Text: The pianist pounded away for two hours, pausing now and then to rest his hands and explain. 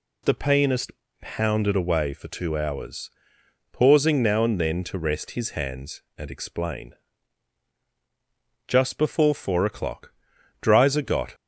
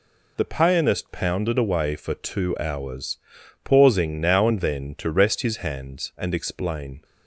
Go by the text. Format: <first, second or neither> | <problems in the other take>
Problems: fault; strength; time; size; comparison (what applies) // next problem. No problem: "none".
second | pauses between "pianist" and "pounded"; slight; at 0.9 s; 0.30 s long // goes on to say "Just before four o'clock Dreiser got"; strong; from 8.6 s on; 2.6 s long